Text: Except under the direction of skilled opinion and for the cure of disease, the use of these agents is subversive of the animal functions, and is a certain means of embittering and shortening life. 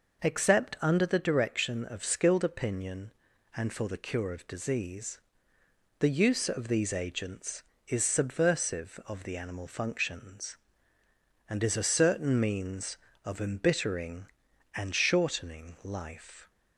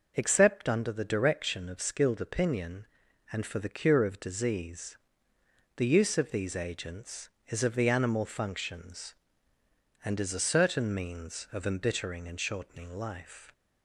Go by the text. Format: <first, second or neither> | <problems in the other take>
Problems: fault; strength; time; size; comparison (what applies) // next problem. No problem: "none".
first | skips "subversive"; at 7.6 s